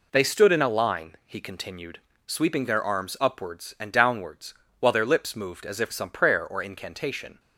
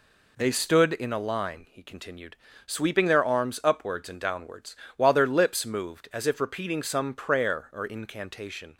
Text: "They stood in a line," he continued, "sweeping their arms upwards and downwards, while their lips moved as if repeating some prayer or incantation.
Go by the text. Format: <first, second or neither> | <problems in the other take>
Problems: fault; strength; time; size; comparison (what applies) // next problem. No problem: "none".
second | skips "repeating"; at 5.9 s